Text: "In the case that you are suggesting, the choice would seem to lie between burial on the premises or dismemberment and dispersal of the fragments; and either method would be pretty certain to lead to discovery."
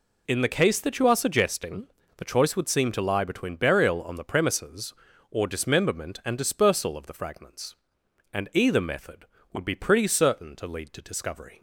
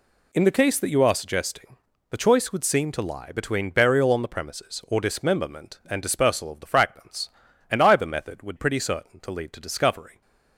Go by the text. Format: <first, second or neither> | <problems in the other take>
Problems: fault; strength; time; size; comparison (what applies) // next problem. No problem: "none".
first | skips "be"; at 8.5 s